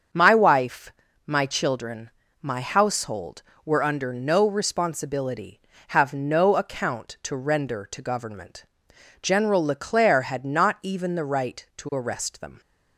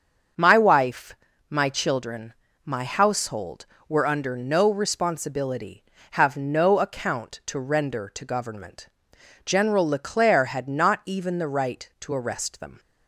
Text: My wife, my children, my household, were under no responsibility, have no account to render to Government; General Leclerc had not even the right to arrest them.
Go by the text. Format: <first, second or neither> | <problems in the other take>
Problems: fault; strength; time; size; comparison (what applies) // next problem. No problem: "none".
neither | starts louder than the rest; strong; the same in both